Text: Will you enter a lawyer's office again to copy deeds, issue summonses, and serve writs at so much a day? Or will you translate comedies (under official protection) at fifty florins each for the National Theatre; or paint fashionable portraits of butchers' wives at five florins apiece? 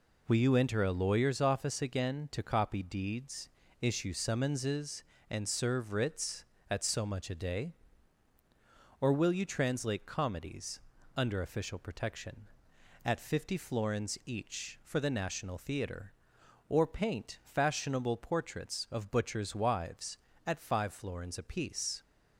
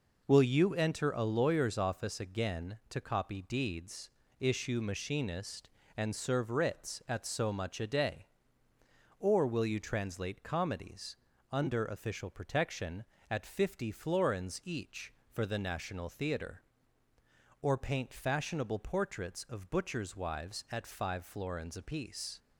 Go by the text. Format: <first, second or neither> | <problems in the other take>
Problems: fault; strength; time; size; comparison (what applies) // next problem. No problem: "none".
first | says "machinist" for "summonses"; at 4.8 s